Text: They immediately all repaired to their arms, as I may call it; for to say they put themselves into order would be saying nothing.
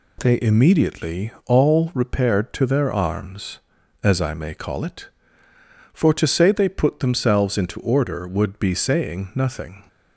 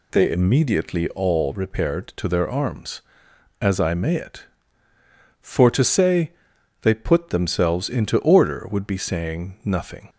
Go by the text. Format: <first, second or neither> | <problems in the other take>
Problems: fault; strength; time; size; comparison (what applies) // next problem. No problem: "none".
first | skips "call"; at 4.1 s // pauses between "say" and "they"; noticeable; at 6.3 s; 0.50 s long